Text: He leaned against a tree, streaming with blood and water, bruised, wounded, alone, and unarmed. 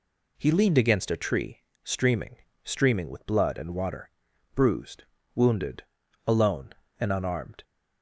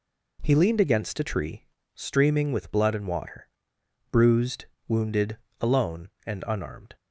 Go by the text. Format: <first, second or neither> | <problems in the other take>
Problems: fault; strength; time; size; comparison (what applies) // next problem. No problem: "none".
second | says "streaming" twice; at 2.6 s